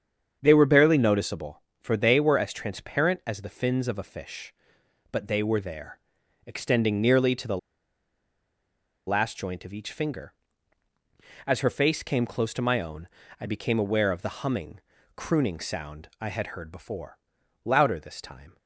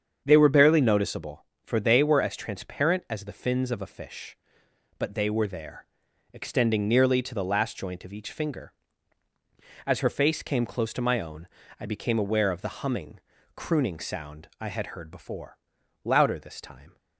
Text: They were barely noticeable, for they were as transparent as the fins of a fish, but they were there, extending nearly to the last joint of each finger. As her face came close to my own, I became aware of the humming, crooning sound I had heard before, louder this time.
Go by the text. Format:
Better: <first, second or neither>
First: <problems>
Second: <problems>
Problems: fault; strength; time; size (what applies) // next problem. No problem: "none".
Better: second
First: starts louder than the rest; strong; until 1.4 s; 7.5 dB // pauses between "the" and "last"; strong; at 7.5 s; 1.4 s long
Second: starts louder than the rest; strong; until 1.2 s; 7.5 dB